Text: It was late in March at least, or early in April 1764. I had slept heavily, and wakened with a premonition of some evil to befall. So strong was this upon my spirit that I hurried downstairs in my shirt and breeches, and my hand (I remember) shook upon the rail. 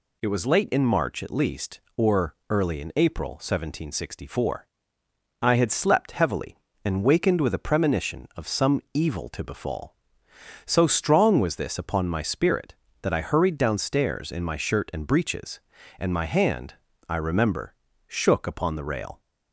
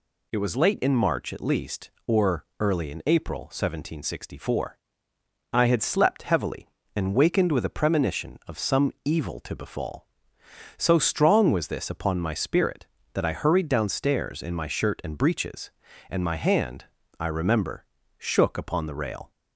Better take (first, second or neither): neither